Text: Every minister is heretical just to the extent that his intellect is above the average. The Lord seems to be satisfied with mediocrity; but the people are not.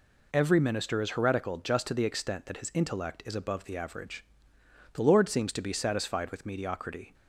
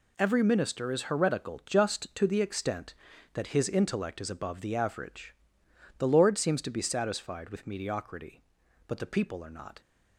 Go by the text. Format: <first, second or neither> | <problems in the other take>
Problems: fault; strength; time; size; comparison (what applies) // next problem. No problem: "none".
second | stops before "but the people are not"; at 7.1 s